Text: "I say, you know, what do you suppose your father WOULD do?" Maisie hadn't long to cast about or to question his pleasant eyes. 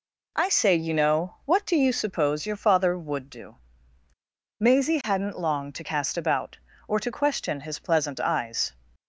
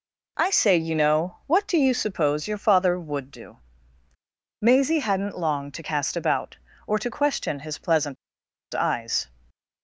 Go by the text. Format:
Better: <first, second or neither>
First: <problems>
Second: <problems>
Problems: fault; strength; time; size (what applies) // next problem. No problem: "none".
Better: first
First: none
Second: pauses between "pleasant" and "eyes"; noticeable; at 8.1 s; 0.57 s long